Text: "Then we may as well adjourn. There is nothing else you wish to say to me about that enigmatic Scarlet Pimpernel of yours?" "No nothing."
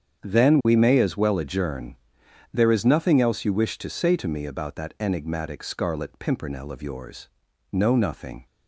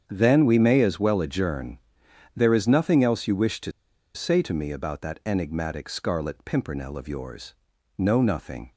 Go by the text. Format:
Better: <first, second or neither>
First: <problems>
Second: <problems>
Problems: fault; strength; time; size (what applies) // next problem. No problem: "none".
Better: first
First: starts louder than the rest; strong; until 1.2 s; 8 dB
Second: starts louder than the rest; strong; until 1.0 s; 8 dB // pauses between "to" and "say"; at 3.7 s; 0.44 s long